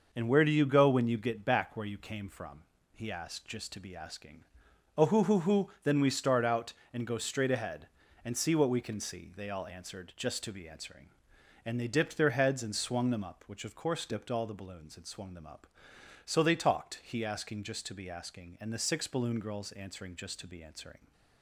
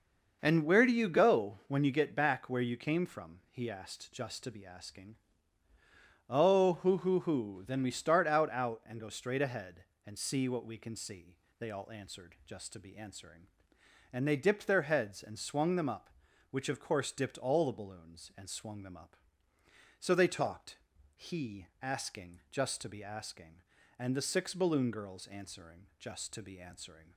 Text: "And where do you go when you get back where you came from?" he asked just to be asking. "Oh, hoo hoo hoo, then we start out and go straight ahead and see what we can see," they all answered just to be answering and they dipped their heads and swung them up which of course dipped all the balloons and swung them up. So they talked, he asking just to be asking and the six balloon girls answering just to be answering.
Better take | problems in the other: first | says "out" twice; at 8.4 s

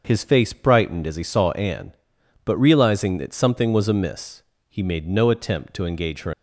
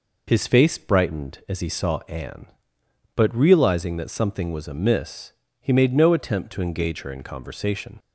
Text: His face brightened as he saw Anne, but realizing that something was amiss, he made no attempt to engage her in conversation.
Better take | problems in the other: second | starts louder than the rest; until 1.0 s; 6.5 dB // stops before "in conversation"; at 6.3 s

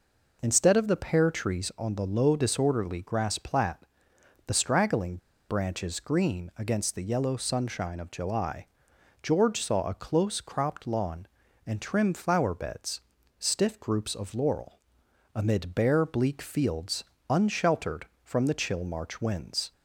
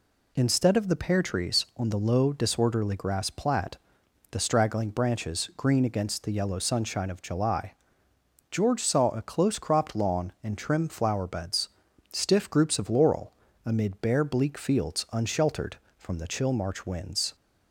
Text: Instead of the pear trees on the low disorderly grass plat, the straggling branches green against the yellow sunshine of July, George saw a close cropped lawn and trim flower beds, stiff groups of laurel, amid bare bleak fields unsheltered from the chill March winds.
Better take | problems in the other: second | pauses between "straggling" and "branches"; slight; at 5.1 s; 0.31 s long // pauses between "fields" and "unsheltered"; slight; at 17.0 s; 0.26 s long

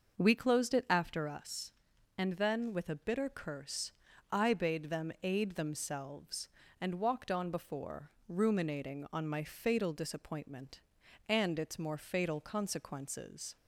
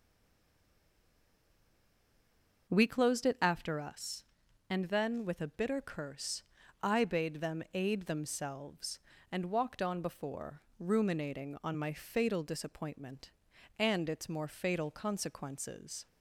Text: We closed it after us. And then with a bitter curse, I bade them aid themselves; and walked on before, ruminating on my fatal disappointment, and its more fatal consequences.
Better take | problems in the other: first | stays silent before the first word; strong; until 2.6 s; 2.6 s long

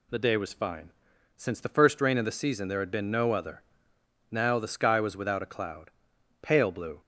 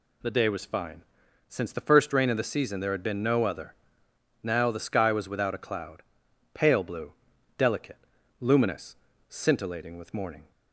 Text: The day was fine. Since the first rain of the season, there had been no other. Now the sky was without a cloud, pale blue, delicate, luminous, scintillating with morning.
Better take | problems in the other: second | stops before "delicate luminous scintillating with morning"; at 7.0 s

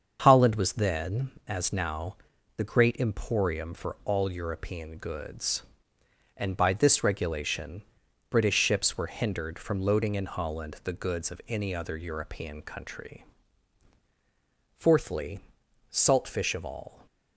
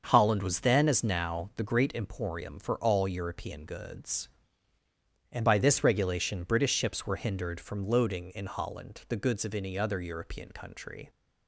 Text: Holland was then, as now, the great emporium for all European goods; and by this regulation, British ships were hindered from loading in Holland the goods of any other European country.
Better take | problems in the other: second | starts louder than the rest; until 1.2 s; 6.5 dB; also in the second // goes on to say "Fourthly Salt fish of all"; strong; from 14.7 s on; 2.3 s long

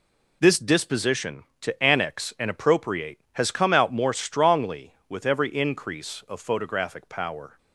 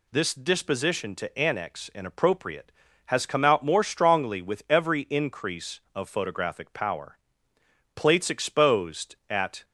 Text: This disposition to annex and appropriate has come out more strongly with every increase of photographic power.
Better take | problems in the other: first | goes on to say "Plates exposed at"; strong; from 7.9 s on; 1.7 s long

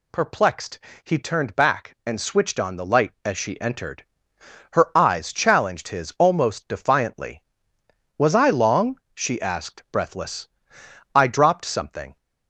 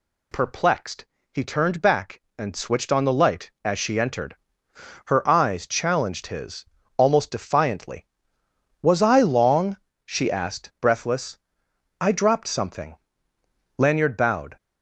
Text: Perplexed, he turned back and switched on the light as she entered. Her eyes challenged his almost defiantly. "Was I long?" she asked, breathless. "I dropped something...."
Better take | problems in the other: first | pauses between "his" and "almost"; slight; at 6.6 s; 0.32 s long // goes on to say "Lanyard bowed"; noticeable; from 13.7 s on; 0.80 s long

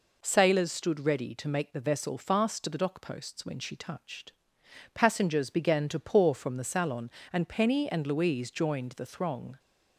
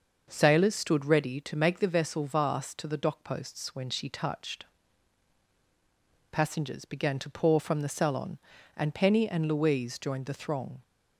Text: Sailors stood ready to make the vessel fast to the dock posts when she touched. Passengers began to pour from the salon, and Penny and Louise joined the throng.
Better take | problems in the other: first | starts louder than the rest; until 1.3 s; 6 dB // says "vast" for "fast"; at 2.2 s

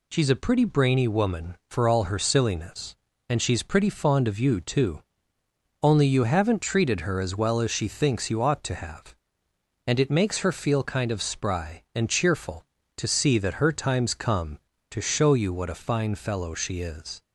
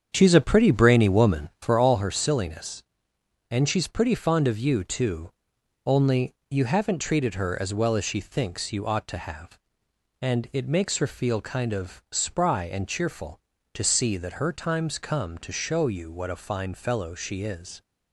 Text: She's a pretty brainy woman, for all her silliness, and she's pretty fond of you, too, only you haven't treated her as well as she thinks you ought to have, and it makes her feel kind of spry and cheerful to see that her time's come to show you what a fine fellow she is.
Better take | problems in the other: first | starts louder than the rest; strong; until 2.0 s; 7.5 dB // pauses between "only" and "you"; slight; at 6.3 s; 0.16 s long

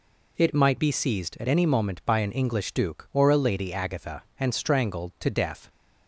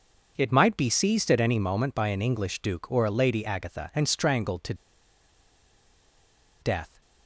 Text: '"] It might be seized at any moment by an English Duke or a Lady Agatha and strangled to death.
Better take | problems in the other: first | pauses between "to" and "death"; strong; at 4.7 s; 1.8 s long

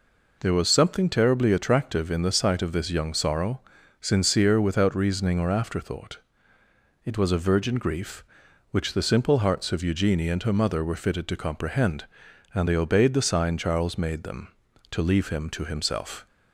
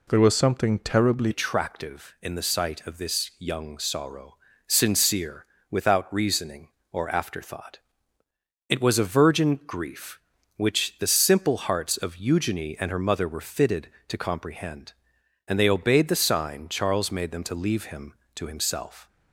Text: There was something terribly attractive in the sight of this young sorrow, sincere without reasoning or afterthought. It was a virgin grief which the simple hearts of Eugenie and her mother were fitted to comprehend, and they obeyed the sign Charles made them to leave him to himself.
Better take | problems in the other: first | changes voice at "attractive"; from 1.3 s on; 17.7 s long // pauses between "sincere" and "without"; slight; at 5.4 s; 0.24 s long

